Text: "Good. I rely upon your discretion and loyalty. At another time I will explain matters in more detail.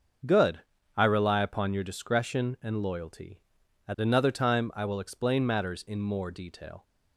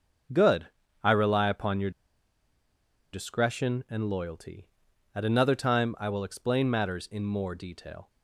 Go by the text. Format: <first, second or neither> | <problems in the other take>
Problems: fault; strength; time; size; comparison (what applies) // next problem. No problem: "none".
first | starts louder than the rest; until 1.7 s; 7 dB; strong in the first // pauses between "your" and "discretion"; at 1.9 s; 1.2 s long